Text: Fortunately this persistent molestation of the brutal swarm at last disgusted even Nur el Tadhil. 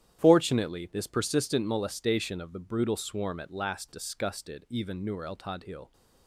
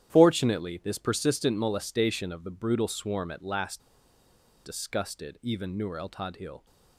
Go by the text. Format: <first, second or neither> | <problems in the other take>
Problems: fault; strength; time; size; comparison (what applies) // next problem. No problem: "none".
first | starts louder than the rest; strong; until 1.1 s; 10.5 dB; strong in the first // pauses between "last" and "disgusted"; noticeable; at 3.7 s; 0.85 s long